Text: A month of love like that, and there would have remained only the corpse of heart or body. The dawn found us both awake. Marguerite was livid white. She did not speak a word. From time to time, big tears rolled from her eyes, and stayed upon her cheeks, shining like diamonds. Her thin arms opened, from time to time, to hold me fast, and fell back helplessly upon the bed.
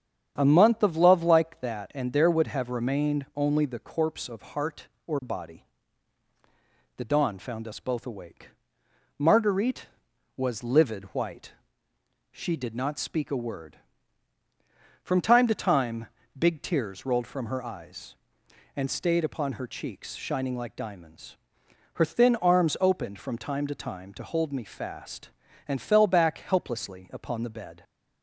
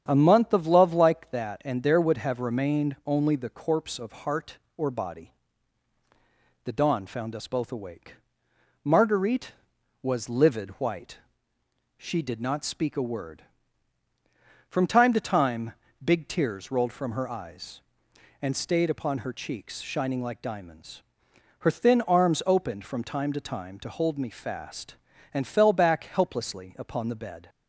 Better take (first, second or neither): neither